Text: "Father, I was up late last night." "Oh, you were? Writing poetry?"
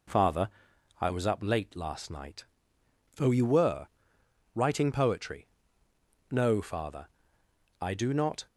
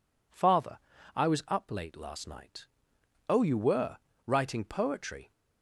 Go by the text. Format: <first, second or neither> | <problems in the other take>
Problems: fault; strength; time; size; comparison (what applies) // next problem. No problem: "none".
second | goes on to say "No Father I do not"; strong; from 6.3 s on; 2.1 s long